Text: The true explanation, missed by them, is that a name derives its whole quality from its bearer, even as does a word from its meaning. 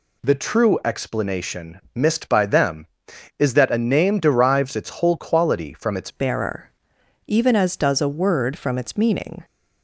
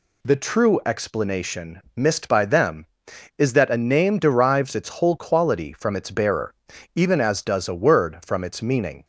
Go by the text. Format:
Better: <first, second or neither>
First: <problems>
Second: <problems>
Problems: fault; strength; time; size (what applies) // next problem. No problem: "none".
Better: second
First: changes voice at "bearer"; from 6.0 s on; 3.4 s long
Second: none